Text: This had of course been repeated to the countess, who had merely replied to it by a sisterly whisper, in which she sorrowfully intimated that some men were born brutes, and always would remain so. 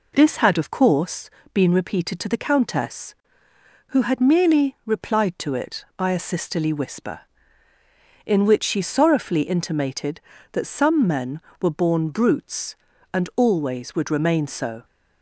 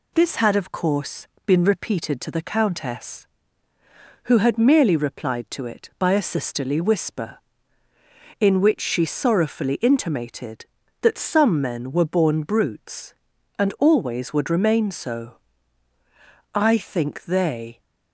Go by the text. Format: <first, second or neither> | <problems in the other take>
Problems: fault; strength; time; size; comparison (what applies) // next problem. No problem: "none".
first | pauses between "course" and "been"; slight; at 1.2 s; 0.20 s long; slight in the first // goes on to say "I think they"; noticeable; from 16.5 s on; 1.2 s long